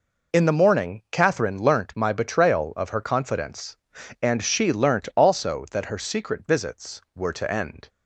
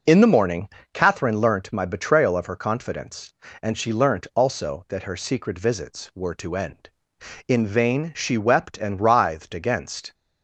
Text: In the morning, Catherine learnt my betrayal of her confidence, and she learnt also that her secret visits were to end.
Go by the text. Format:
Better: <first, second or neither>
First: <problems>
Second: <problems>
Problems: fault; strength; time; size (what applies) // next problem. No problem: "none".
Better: first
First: none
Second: goes on to say "In vain she wept and writhed against"; strong; from 7.4 s on; 2.6 s long